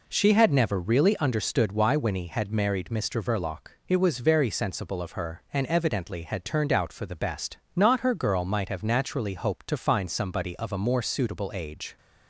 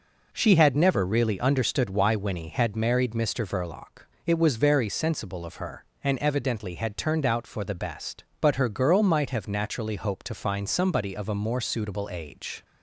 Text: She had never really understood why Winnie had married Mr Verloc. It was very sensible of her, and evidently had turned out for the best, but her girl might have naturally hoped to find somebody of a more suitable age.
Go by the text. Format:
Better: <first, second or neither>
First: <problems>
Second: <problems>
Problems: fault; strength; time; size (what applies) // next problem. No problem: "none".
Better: second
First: says "not" for "but"; at 7.7 s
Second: none